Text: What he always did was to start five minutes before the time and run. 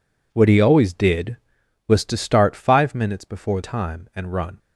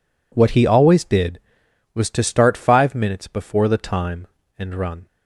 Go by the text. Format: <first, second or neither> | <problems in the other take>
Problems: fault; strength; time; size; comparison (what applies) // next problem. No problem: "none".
second | skips "the"; at 3.6 s